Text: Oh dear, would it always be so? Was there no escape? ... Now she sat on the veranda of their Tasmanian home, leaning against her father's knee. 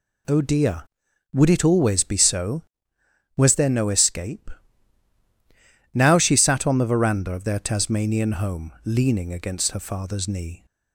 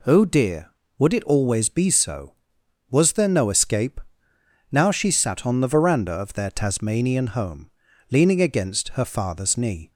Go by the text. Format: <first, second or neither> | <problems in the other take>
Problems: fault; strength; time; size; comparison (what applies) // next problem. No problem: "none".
neither | none